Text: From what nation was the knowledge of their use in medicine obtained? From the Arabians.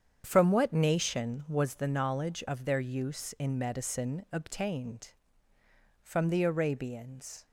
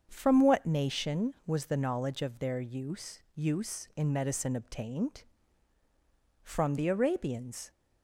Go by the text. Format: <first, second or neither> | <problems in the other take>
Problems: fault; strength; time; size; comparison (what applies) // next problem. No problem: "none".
first | starts louder than the rest; until 1.1 s; 7 dB; strong in the first // says "use" twice; at 3.3 s